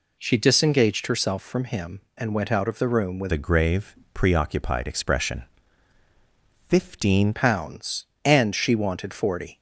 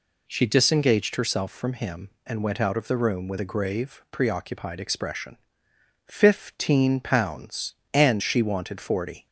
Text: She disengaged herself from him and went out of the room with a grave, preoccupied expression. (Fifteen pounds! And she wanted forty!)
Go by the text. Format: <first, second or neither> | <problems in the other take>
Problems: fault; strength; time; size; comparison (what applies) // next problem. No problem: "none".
second | changes voice from "a" to "Fifteen"; from 3.3 to 7.3 s; 4.0 s long